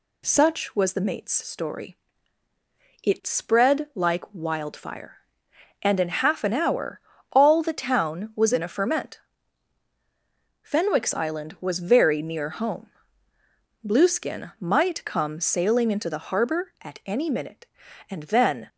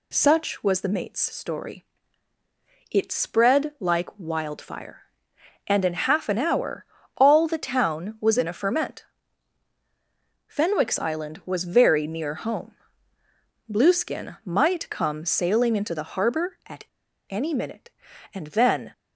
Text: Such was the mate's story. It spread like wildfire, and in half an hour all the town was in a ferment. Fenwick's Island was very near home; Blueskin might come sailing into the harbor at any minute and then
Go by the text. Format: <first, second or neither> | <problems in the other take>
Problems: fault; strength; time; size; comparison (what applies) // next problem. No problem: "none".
first | pauses between "hour" and "all"; slight; at 6.8 s; 0.32 s long; slight in the first // pauses between "at" and "any"; at 16.8 s; 0.45 s long